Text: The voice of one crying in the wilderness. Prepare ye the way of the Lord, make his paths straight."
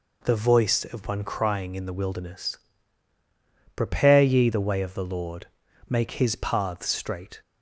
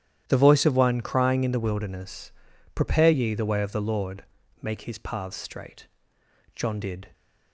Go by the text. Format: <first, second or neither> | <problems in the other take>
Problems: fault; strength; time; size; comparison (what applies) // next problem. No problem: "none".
first | starts louder than the rest; strong; until 1.2 s; 11 dB // goes on to say "John did"; from 6.5 s on; 0.58 s long